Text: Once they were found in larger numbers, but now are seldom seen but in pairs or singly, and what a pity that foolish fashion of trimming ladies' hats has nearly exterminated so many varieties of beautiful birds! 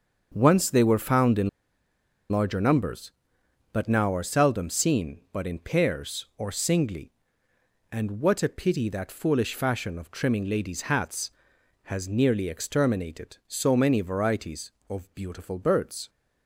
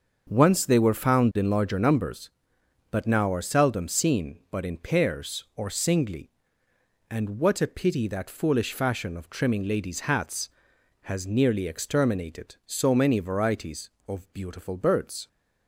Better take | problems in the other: second | starts louder than the rest; until 1.3 s; 6.5 dB; also in the second // pauses between "in" and "larger"; noticeable; at 1.4 s; 0.81 s long

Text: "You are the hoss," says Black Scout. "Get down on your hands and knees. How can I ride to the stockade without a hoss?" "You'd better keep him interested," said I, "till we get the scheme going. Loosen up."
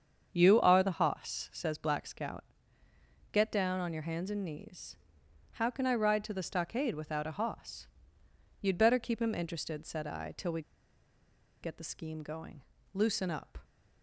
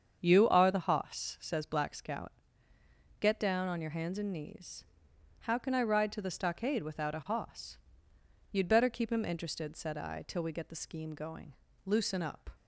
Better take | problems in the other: second | starts louder than the rest; strong; until 1.3 s; 7.5 dB; strong in the second // pauses between "we" and "get"; at 10.6 s; 1.0 s long

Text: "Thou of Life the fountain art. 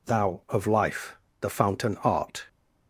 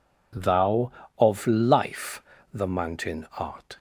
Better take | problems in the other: first | pauses between "Life" and "the"; slight; at 2.1 s; 0.32 s long; slight in the first // says "mountain" for "fountain"; at 2.6 s

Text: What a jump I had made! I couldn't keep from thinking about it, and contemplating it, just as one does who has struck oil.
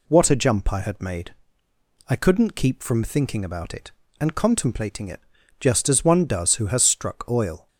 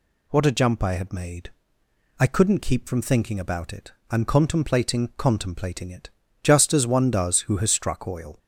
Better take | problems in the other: first | says "contemplating" twice; at 5.1 s

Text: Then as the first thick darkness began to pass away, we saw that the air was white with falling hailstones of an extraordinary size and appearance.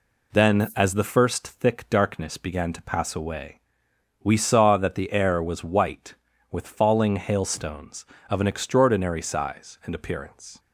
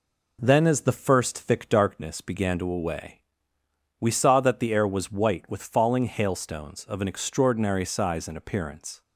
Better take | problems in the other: first | skips "pass"; at 2.7 s

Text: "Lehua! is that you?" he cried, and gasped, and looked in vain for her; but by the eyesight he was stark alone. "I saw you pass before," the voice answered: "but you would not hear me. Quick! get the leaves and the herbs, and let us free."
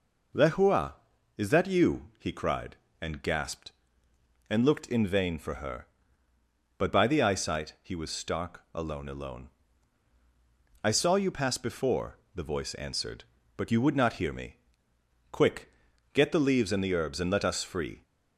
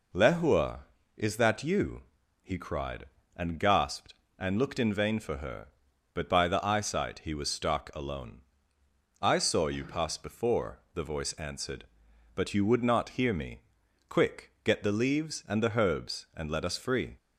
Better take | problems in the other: second | says "alone" twice; at 9.0 s

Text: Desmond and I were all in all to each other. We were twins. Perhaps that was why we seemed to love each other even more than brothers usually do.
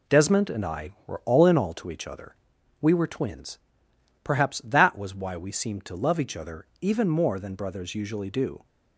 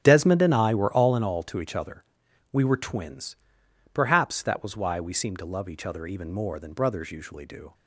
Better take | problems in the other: first | starts louder than the rest; strong; until 1.2 s; 8.5 dB

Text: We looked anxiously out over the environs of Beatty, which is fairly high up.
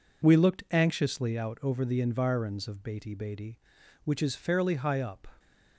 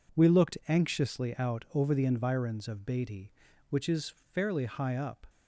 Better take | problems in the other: second | says "Beatty" twice; at 3.1 s

